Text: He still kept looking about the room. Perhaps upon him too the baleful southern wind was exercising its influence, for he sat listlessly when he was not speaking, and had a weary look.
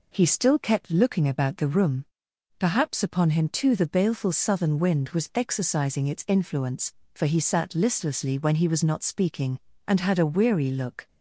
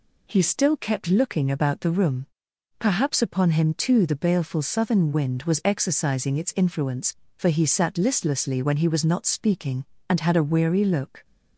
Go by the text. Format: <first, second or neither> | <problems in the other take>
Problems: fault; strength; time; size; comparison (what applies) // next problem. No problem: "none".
neither | none